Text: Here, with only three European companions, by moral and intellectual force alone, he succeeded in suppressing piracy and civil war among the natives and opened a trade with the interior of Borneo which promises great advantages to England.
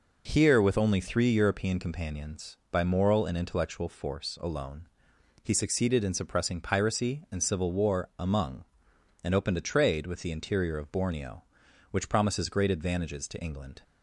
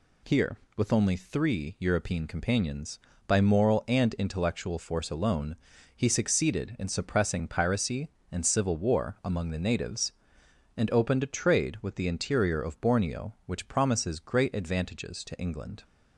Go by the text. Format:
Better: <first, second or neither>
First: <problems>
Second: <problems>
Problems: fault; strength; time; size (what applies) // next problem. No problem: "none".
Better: second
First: skips "the natives"; at 8.9 s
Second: none